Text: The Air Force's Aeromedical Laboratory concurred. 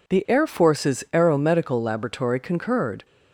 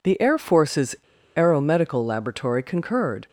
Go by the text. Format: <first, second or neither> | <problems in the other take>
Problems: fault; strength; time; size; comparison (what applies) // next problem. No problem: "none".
first | pauses between "Force's" and "Aeromedical"; at 0.9 s; 0.39 s long